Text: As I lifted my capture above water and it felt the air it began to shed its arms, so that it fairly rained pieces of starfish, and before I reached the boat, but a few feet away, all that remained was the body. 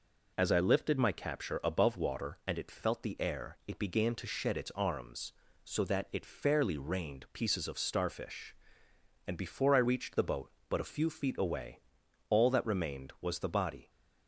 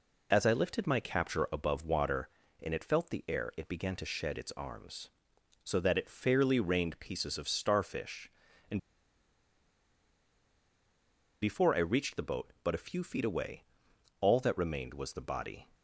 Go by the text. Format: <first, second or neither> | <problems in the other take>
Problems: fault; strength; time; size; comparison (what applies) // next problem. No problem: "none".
first | pauses between "and" and "before"; strong; at 8.7 s; 2.6 s long